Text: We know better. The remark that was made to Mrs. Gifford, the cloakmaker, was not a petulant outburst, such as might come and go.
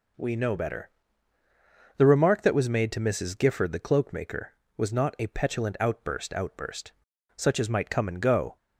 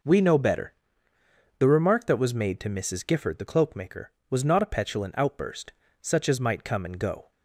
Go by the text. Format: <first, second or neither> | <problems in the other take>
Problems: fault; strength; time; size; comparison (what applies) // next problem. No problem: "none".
second | says "outburst" twice; at 6.3 s